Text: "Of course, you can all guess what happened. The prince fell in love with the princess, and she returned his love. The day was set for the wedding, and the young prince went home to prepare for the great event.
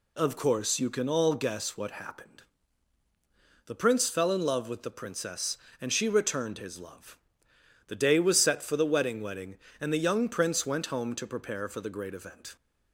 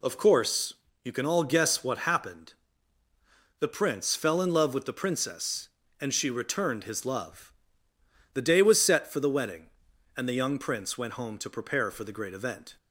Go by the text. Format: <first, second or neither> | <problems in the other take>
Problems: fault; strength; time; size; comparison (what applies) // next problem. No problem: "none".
second | says "wedding" twice; at 9.2 s